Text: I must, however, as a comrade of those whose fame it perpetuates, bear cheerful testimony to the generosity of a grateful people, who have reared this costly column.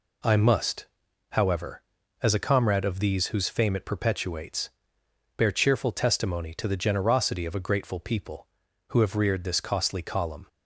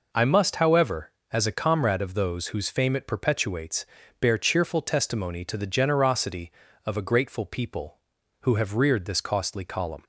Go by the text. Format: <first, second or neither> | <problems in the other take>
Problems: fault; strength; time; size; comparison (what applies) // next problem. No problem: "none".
second | says "these" for "those"; at 2.9 s